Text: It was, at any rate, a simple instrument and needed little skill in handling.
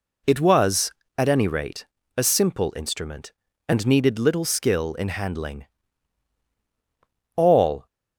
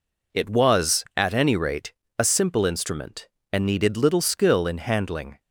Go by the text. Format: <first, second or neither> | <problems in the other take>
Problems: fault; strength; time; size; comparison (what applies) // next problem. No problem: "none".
second | goes on to say "All"; from 7.3 s on; 0.50 s long